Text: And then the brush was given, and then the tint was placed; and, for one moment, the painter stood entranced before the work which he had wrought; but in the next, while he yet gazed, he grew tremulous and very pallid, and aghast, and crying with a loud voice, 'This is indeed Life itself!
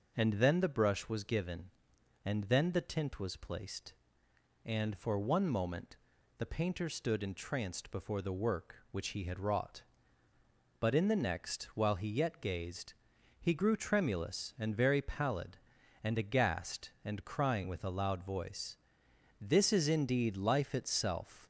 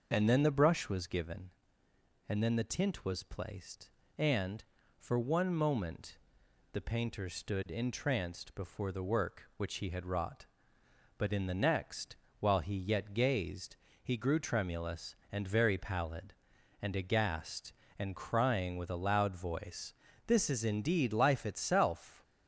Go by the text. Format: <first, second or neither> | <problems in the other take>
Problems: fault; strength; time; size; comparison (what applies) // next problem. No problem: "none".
neither | none